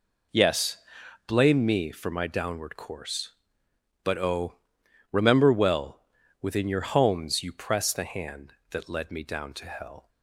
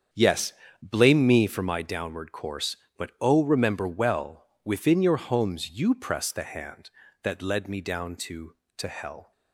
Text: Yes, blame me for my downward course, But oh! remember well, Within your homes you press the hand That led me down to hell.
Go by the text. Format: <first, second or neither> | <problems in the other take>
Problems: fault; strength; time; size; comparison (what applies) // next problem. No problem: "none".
first | starts louder than the rest; strong; until 1.4 s; 8 dB // says "to" twice; at 8.7 s